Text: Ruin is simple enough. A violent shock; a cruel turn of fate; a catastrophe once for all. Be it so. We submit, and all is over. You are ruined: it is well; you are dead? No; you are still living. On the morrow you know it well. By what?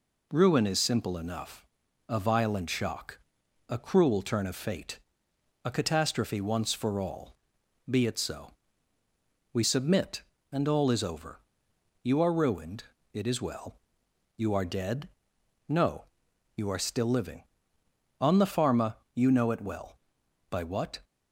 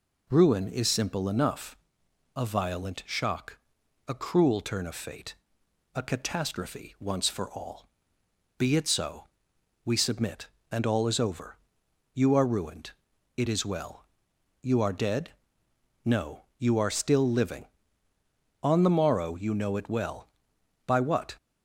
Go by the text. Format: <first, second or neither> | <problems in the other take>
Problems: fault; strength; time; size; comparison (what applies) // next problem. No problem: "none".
second | says "pharma" for "morrow"; at 18.5 s